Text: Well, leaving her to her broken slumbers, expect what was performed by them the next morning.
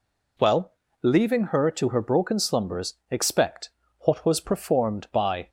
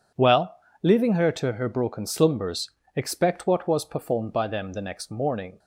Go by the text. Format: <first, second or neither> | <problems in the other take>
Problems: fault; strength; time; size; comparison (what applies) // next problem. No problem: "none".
second | pauses between "expect" and "what"; slight; at 3.6 s; 0.32 s long // stops before "them the next morning"; at 5.4 s